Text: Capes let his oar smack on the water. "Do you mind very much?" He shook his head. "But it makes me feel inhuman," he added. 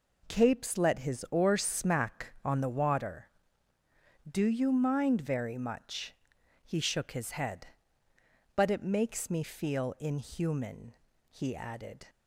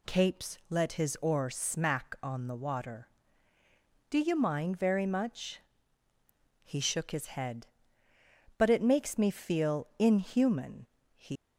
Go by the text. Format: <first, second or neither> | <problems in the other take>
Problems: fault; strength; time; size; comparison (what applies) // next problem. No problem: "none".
first | stops before "added"; at 11.3 s